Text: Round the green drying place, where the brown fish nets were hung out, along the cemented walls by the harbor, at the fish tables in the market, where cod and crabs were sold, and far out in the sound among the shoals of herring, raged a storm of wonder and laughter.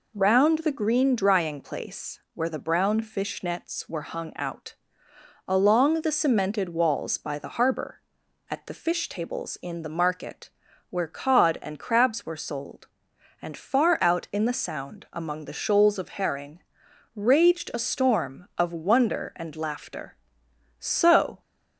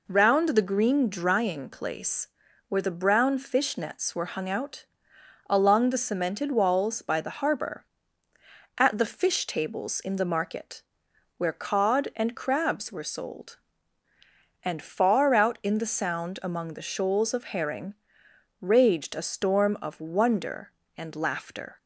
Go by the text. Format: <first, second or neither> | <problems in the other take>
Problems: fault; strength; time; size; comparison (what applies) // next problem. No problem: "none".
second | goes on to say "So"; from 20.8 s on; 0.60 s long